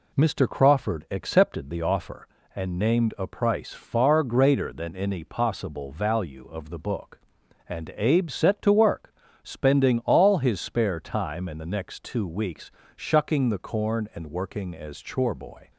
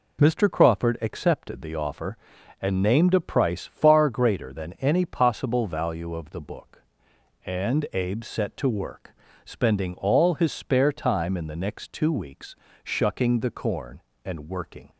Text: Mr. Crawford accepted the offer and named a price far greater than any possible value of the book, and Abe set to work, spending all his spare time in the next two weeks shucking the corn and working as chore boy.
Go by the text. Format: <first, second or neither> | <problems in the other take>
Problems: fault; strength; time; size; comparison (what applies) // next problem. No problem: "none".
first | pauses between "weeks" and "shucking"; slight; at 12.5 s; 0.30 s long; slight in the first // stops before "as chore boy"; at 14.8 s